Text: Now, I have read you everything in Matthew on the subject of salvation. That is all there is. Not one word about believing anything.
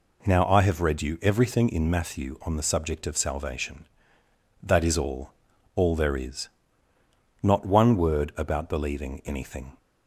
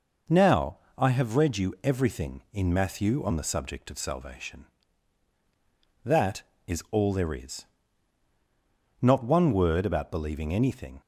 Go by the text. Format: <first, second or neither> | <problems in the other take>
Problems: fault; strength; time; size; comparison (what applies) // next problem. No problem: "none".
second | says "all" twice; at 5.7 s